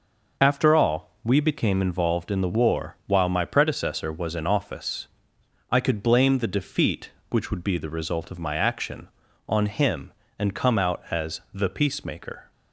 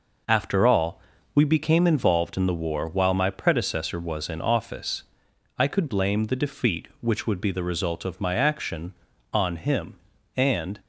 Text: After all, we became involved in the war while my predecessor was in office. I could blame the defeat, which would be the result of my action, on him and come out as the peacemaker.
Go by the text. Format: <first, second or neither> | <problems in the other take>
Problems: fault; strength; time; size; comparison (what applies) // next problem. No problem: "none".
first | stops before "come out as the peacemaker"; at 10.7 s